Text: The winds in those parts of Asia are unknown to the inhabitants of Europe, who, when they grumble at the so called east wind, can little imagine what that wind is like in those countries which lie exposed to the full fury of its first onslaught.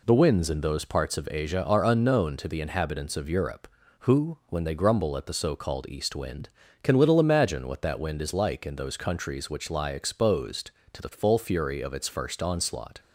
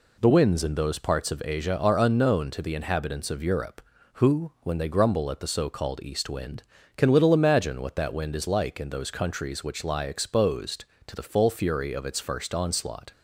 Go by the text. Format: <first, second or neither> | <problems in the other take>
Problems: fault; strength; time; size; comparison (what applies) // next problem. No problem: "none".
neither | none